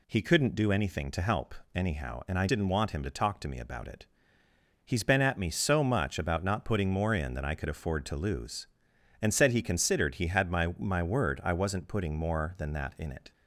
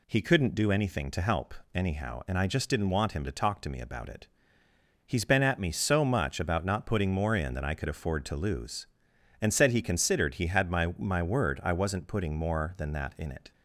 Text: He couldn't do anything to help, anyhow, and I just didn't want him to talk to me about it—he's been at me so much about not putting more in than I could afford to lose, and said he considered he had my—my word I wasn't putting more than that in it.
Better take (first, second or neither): second